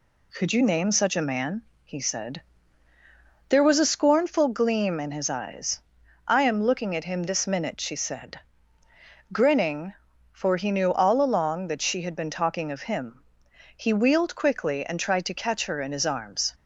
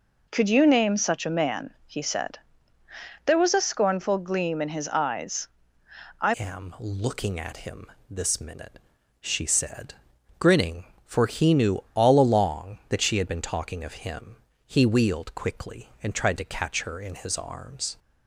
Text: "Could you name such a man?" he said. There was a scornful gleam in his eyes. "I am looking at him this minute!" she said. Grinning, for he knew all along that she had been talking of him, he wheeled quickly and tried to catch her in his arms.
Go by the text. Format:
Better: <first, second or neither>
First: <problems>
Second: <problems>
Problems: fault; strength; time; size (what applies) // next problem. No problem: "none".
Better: first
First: none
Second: changes voice at "am"; from 6.3 s on; 11.6 s long // pauses between "him" and "this"; slight; at 7.8 s; 0.22 s long